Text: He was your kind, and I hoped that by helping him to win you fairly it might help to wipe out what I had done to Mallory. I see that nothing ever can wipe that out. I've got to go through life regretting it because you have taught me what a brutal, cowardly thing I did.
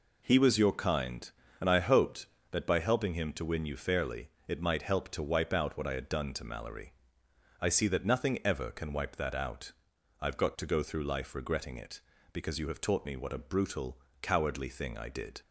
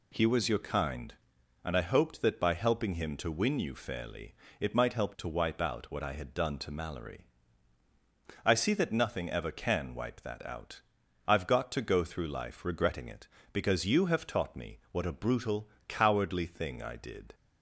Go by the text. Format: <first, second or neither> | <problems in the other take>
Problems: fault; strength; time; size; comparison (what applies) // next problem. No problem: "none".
neither | pauses between "fairly" and "it"; slight; the same in both